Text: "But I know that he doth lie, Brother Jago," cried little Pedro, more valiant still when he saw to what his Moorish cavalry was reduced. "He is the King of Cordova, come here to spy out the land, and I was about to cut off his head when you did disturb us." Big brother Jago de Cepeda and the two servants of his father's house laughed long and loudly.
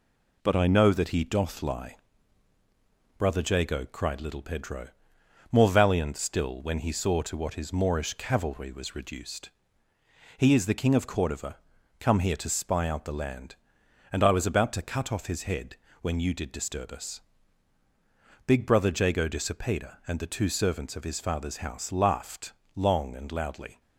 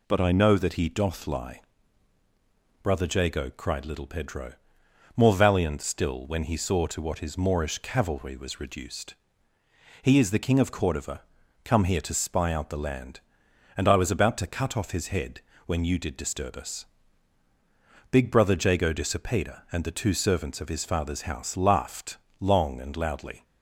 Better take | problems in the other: second | gets quieter; throughout; 3.5 dB // pauses between "head" and "when"; slight; at 15.7 s; 0.24 s long; slight in the second // pauses between "laughed" and "long"; slight; at 22.5 s; 0.20 s long; slight in the second

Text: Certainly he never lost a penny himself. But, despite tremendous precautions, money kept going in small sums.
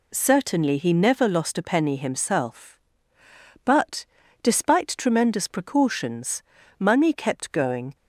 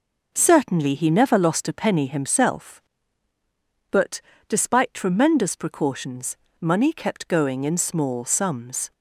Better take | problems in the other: second | stops before "in small sums"; at 7.9 s

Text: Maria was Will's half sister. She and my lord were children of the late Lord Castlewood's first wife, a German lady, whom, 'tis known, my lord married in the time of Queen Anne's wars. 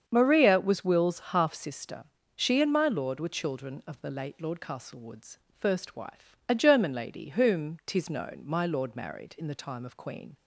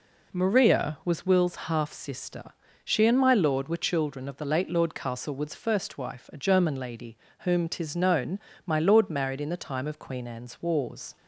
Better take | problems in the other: second | starts louder than the rest; strong; until 1.0 s; 7 dB // pauses between "Castlewood's" and "first"; slight; at 5.3 s; 0.22 s long // stops before "Anne's wars"; at 10.3 s

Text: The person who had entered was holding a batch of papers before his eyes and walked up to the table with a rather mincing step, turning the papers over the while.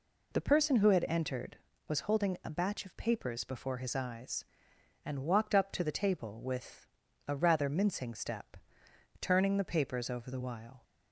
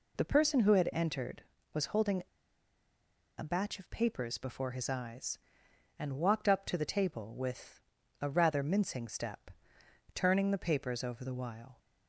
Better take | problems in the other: first | pauses between "holding" and "a"; at 2.2 s; 1.1 s long // pauses between "with" and "a"; at 7.8 s; 0.40 s long; also in the first

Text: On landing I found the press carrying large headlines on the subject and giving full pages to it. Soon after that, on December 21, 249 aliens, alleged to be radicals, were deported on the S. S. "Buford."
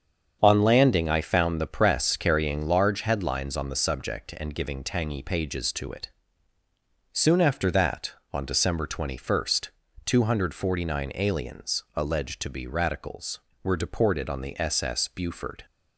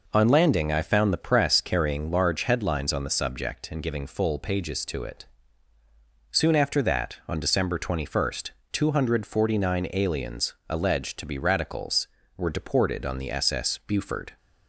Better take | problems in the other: second | starts louder than the rest; strong; until 1.4 s; 7.5 dB // says "tangy" for "full"; at 4.8 s

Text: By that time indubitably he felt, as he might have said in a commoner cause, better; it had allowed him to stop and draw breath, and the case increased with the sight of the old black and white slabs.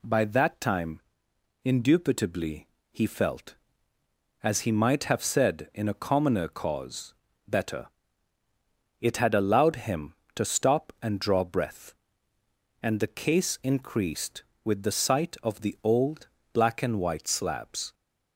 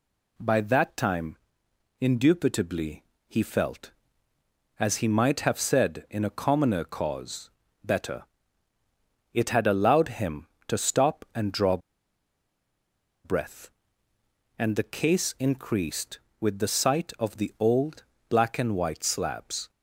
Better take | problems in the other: first | pauses between "time" and "indubitably"; noticeable; at 1.3 s; 0.62 s long; noticeable in the first // pauses between "indubitably" and "he"; slight; at 3.0 s; 0.24 s long; slight in the first // pauses between "draw" and "breath"; strong; at 11.7 s; 1.4 s long // pauses between "old" and "black"; slight; at 18.0 s; 0.24 s long; slight in the first

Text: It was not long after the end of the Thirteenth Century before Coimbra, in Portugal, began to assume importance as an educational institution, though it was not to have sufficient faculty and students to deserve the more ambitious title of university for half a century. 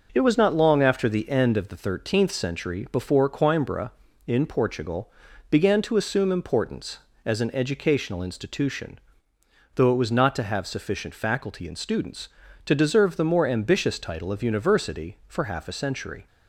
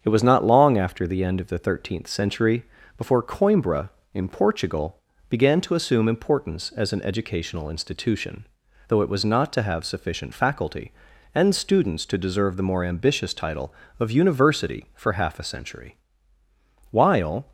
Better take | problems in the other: first | starts louder than the rest; strong; until 1.0 s; 7.5 dB // pauses between "Century" and "before"; slight; at 2.6 s; 0.32 s long // goes on to say "While"; from 16.9 s on; 0.60 s long

